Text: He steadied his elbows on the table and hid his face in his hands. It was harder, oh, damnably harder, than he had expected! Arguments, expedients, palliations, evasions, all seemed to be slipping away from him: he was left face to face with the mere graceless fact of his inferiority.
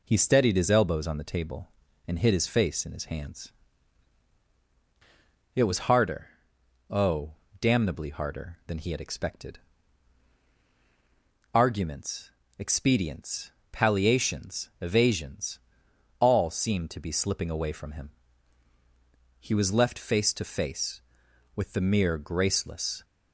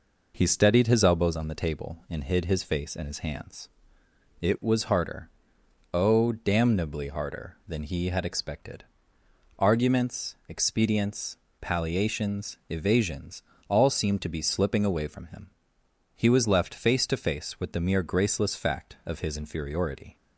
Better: second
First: stops before "fact of his inferiority"; at 23.0 s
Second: none

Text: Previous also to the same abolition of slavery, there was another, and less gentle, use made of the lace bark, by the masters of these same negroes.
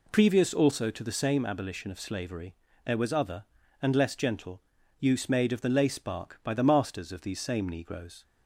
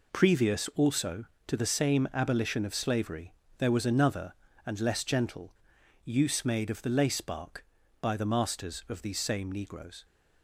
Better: second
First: says "other" for "another"; at 3.1 s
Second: none

